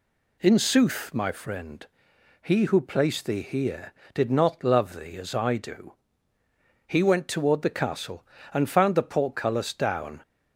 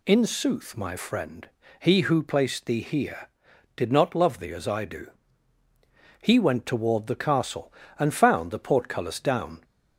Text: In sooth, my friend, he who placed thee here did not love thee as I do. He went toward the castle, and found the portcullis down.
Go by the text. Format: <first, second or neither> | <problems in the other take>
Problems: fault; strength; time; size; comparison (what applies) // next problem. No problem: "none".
neither | none